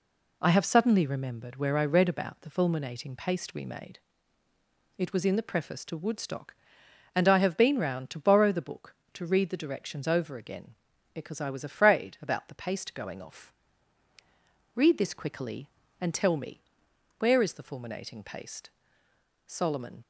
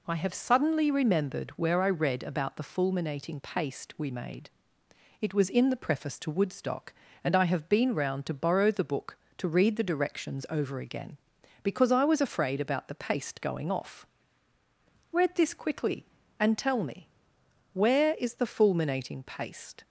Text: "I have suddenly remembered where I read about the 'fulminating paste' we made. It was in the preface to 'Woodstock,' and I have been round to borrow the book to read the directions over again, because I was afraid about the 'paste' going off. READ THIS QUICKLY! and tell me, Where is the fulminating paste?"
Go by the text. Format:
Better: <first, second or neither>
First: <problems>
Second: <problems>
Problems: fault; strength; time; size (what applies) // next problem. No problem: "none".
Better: second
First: goes on to say "Solomon"; from 19.4 s on; 0.58 s long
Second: none